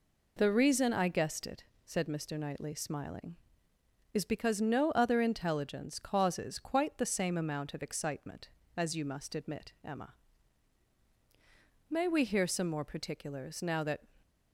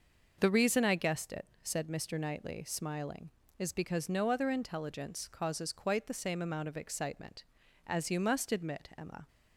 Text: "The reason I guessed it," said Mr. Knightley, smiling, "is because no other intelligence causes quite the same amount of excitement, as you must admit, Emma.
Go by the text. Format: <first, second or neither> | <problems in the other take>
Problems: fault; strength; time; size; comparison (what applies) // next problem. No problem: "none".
second | goes on to say "May we hear some more particulars now that"; strong; from 11.8 s on; 2.1 s long